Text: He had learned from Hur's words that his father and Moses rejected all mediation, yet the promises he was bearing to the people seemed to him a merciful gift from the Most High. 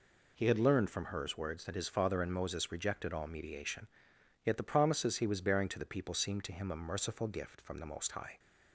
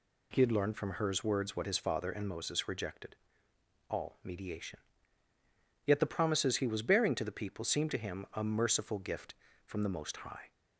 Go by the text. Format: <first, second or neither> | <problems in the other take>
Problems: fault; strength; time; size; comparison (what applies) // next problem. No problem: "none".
first | says "what" for "that"; at 1.5 s // pauses between "rejected" and "all"; noticeable; at 3.1 s; 0.74 s long